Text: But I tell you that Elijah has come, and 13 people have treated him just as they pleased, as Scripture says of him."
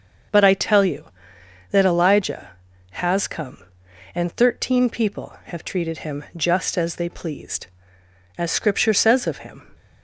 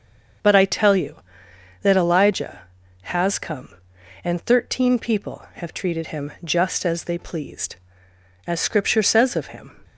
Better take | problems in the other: neither | starts louder than the rest; the same in both

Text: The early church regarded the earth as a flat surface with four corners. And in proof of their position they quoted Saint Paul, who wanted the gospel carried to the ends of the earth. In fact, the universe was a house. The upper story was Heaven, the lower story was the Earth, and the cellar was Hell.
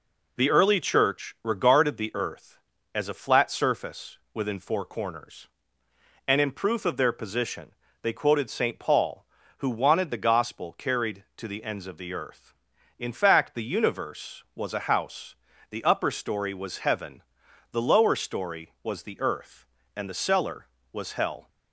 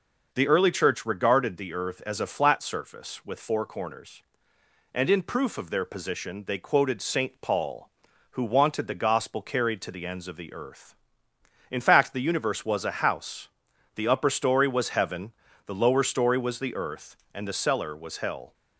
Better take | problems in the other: second | says "within" for "with"; at 4.3 s // pauses between "position" and "they"; slight; at 7.6 s; 0.32 s long

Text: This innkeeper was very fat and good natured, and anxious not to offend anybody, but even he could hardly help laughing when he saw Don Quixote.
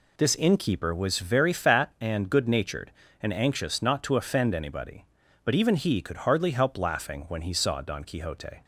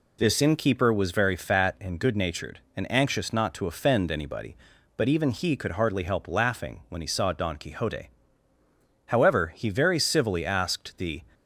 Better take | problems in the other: first | goes on to say "However he very civilly asked the"; strong; from 9.0 s on; 2.1 s long

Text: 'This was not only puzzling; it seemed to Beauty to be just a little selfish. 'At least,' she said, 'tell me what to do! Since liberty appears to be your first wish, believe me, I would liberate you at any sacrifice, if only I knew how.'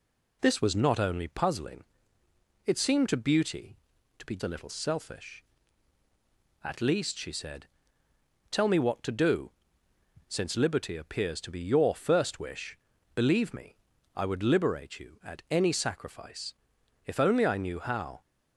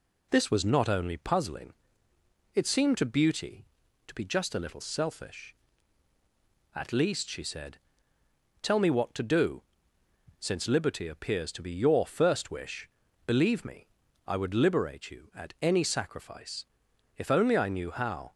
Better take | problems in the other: second | skips "just"; at 4.3 s

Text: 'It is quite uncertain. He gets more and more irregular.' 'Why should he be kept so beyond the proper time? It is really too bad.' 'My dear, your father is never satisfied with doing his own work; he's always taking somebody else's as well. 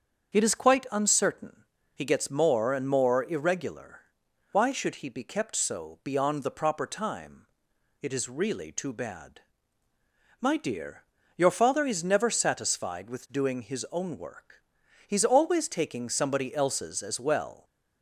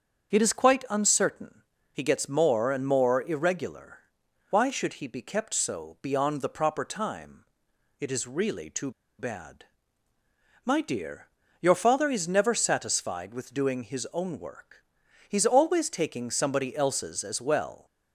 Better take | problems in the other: first | starts louder than the rest; strong; until 1.3 s; 7 dB; strong in the first // pauses between "too" and "bad"; slight; at 8.9 s; 0.27 s long

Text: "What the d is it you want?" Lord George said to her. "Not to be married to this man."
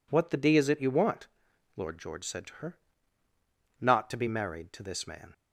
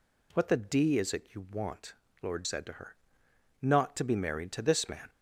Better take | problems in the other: first | skips "George"; at 2.4 s

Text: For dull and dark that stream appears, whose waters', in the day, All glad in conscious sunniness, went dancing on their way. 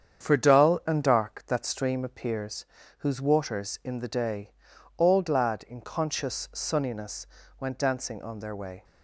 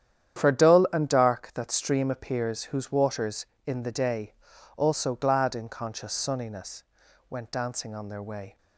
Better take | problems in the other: first | starts louder than the rest; strong; until 1.4 s; 10 dB; strong in the first // says "Also" for "All"; at 4.7 s

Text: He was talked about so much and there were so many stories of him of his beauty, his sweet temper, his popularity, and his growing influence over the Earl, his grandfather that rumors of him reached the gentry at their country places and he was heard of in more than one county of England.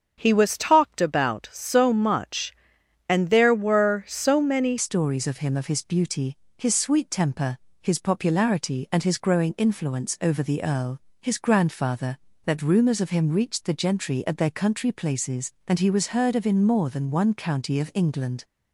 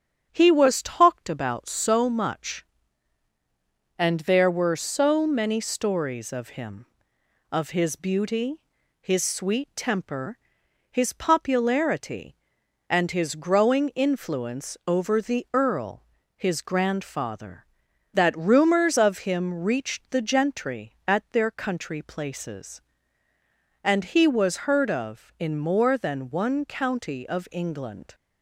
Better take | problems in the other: second | starts louder than the rest; until 1.2 s; 7 dB; strong in the second // changes voice at "stories"; from 4.7 s on; 13.7 s long

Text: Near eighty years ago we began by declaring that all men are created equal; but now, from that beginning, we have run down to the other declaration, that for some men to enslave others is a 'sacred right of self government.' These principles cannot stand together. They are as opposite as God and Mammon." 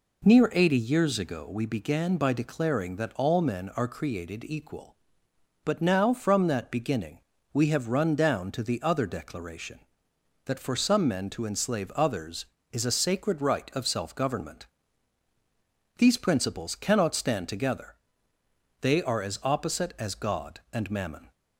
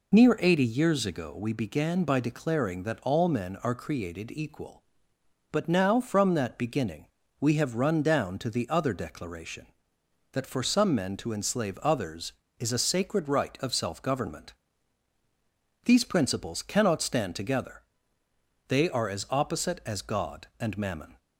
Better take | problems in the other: first | loses the start of "Near"; at 0.1 s; 30 ms

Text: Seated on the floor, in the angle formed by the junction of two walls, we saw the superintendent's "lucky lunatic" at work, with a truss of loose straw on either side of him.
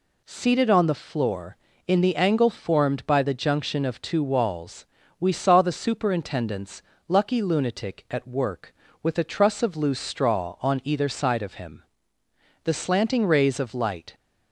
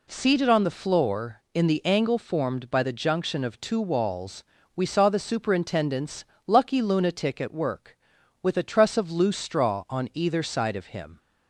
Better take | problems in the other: second | pauses between "superintendent's" and "lucky"; slight; at 6.8 s; 0.28 s long; slight in the second // goes on to say "The slanting rays of light"; from 12.6 s on; 1.5 s long

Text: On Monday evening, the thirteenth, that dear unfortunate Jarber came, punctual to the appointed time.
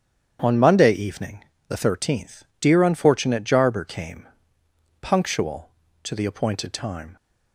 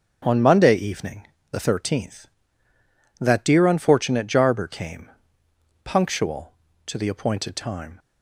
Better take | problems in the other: second | starts louder than the rest; strong; until 1.4 s; 8.5 dB; strong in the second // skips "that"; at 2.5 s

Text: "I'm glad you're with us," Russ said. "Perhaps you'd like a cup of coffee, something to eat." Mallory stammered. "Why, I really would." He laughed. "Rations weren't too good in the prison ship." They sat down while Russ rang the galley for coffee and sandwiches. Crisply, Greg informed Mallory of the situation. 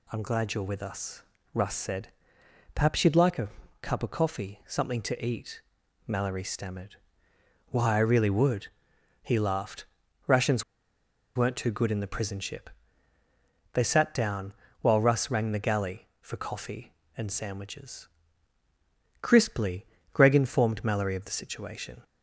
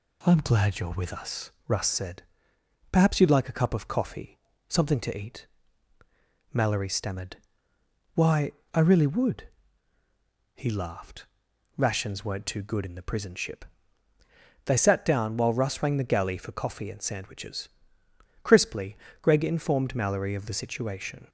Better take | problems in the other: second | pauses between "a" and "cup"; slight; at 3.4 s; 0.32 s long // pauses between "Rations" and "weren't"; noticeable; at 10.6 s; 0.72 s long // pauses between "down" and "while"; slight; at 14.5 s; 0.28 s long

